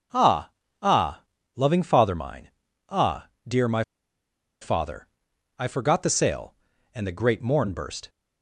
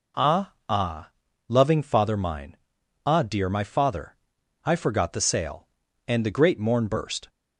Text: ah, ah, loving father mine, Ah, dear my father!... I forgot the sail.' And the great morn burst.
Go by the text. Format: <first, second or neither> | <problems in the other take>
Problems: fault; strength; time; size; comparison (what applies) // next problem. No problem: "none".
second | pauses between "my" and "father"; noticeable; at 3.8 s; 0.77 s long